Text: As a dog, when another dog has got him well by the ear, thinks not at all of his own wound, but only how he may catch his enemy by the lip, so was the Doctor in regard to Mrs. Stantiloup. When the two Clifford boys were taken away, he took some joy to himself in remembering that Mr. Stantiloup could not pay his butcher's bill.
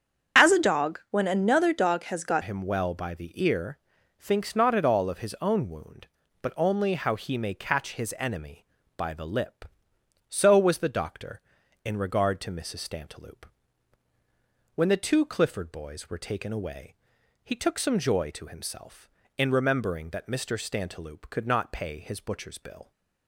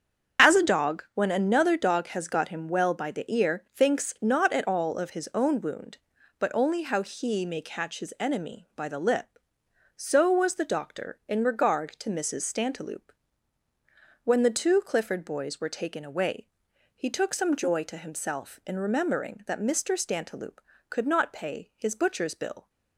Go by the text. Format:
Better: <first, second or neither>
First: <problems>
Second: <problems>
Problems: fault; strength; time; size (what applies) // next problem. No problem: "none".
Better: second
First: starts louder than the rest; until 1.4 s; 6.5 dB // changes voice at "him"; from 2.4 s on; 20.5 s long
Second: starts louder than the rest; noticeable; until 1.5 s; 6 dB